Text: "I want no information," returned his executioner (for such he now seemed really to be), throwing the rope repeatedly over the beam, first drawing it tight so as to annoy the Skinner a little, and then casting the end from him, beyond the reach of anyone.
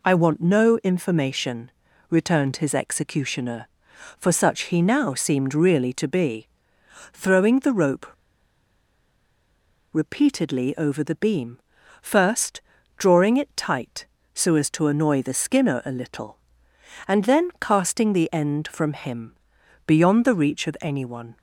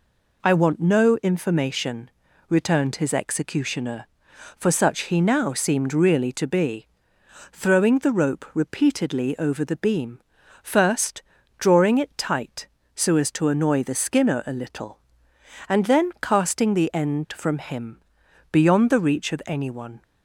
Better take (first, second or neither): second